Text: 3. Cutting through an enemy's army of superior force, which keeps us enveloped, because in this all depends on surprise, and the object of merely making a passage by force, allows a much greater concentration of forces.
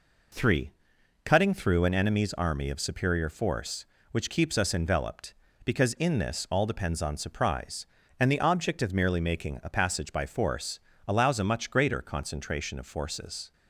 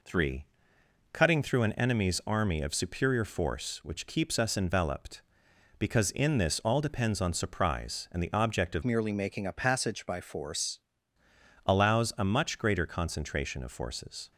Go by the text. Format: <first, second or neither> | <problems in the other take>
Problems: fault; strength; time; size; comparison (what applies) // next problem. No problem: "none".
first | changes voice from "merely" to "force"; from 8.8 to 10.8 s; 2.0 s long